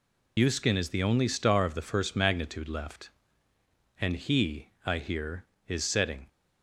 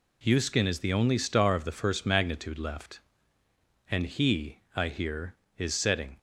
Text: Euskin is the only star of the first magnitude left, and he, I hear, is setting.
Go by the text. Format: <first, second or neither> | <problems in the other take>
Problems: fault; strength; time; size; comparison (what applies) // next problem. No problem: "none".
second | loses the start of "Euskin"; at 0.3 s; 60 ms